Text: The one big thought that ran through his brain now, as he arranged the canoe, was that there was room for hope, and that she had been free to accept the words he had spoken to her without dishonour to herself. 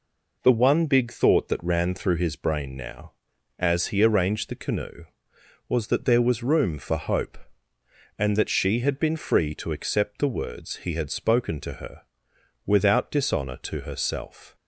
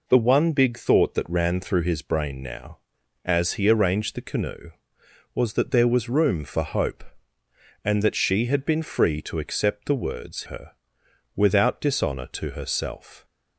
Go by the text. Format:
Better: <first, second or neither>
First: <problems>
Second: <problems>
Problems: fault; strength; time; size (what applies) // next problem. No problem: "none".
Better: first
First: pauses between "her" and "without"; noticeable; at 12.0 s; 0.62 s long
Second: skips "he had spoken to"; at 10.4 s // pauses between "her" and "without"; noticeable; at 10.7 s; 0.62 s long